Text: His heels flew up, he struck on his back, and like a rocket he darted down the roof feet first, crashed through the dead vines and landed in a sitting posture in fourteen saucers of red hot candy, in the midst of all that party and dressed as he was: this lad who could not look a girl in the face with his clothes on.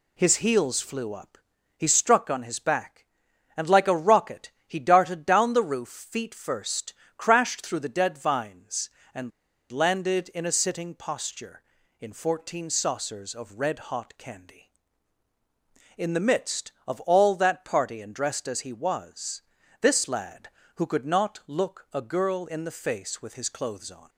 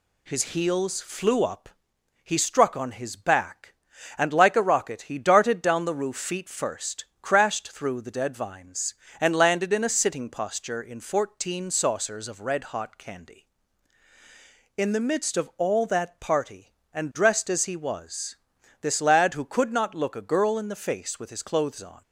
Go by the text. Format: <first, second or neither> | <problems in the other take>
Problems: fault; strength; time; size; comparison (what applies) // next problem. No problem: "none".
second | pauses between "rocket" and "he"; slight; at 4.4 s; 0.16 s long // pauses between "and" and "landed"; at 9.3 s; 0.40 s long